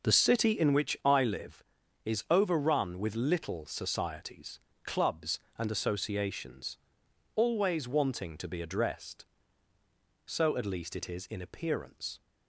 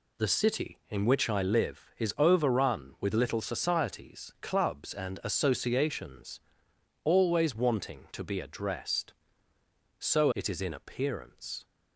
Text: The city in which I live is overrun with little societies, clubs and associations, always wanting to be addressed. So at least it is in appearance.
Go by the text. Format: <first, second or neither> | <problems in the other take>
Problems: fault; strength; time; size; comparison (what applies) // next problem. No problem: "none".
first | skips "at least"; at 10.3 s